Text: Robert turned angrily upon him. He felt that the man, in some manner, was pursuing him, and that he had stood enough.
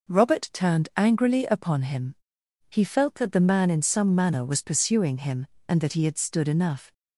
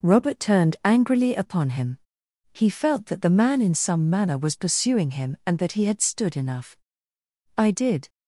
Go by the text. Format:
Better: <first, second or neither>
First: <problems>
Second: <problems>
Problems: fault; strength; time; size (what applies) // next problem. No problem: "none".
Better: first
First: none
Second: goes on to say "I did"; from 7.5 s on; 0.54 s long